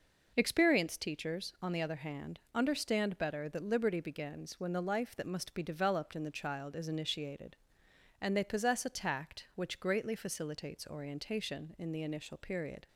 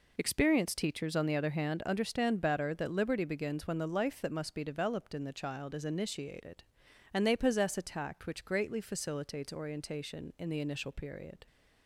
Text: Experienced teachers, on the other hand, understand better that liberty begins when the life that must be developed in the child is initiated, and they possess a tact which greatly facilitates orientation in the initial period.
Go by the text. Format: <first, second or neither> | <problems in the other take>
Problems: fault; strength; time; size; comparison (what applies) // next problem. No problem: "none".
neither | none